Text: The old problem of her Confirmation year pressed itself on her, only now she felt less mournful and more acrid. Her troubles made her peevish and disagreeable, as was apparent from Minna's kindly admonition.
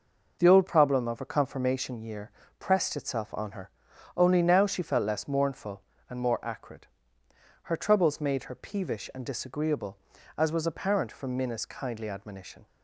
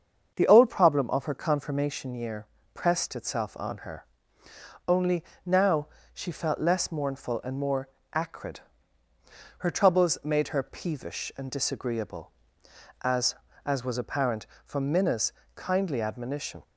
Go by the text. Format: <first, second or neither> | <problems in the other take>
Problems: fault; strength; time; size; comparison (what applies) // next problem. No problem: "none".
first | starts louder than the rest; until 1.3 s; 7 dB // pauses between "year" and "pressed"; slight; at 2.4 s; 0.26 s long; slight in the first // pauses between "only" and "now"; slight; at 5.2 s; 0.22 s long // pauses between "now" and "she"; slight; at 5.8 s; 0.28 s long // pauses between "more" and "acrid"; slight; at 7.8 s; 0.26 s long // says "as" twice; at 13.6 s // pauses between "Minna's" and "kindly"; slight; at 15.3 s; 0.22 s long